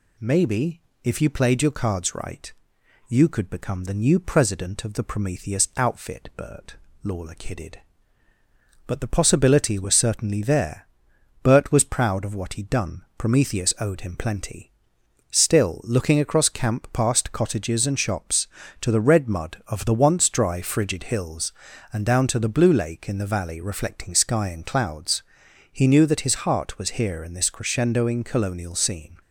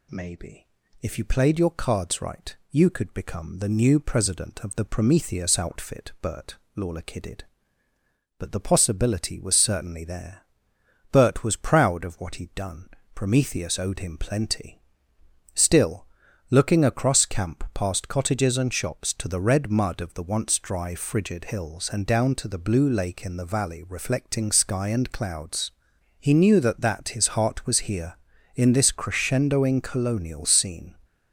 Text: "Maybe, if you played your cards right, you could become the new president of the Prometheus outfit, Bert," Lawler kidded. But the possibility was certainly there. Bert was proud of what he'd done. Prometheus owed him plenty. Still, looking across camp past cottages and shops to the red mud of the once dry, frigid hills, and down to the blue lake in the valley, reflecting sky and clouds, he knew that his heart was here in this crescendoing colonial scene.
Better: first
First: none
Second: says "that" twice; at 26.8 s

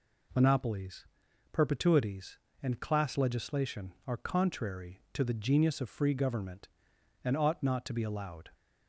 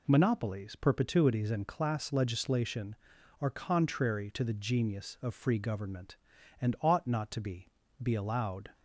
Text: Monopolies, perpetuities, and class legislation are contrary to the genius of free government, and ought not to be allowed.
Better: first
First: none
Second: says "be" twice; at 8.0 s

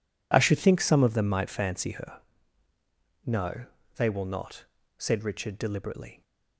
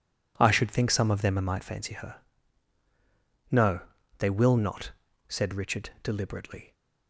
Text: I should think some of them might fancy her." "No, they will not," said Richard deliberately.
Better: neither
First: none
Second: none

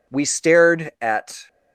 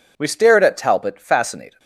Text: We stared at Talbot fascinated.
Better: second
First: stops before "Talbot fascinated"; at 1.4 s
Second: none

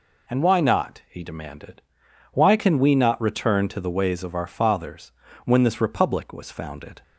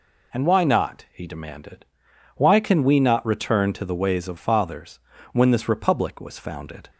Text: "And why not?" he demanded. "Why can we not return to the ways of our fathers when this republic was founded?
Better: first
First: pauses between "fathers" and "when"; slight; at 5.1 s; 0.32 s long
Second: skips "our"; at 4.3 s // pauses between "fathers" and "when"; slight; at 4.9 s; 0.32 s long

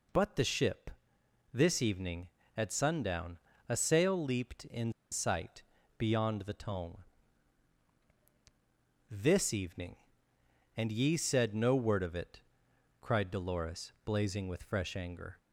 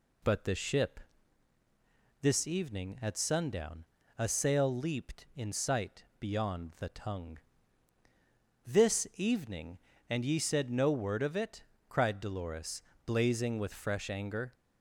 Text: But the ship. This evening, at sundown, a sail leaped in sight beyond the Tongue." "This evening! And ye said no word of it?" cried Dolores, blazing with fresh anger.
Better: second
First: pauses between "in" and "sight"; slight; at 4.9 s; 0.20 s long // pauses between "sight" and "beyond"; slight; at 5.6 s; 0.36 s long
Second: pauses between "sight" and "beyond"; slight; at 6.0 s; 0.16 s long

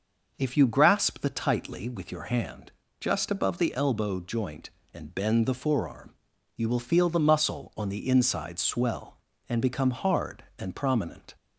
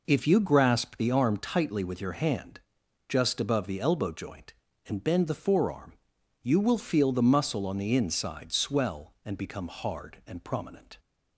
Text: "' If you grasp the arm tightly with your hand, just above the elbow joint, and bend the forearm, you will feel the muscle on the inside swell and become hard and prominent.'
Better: second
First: starts louder than the rest; noticeable; until 1.3 s; 6 dB // skips "arm"; at 1.2 s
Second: none

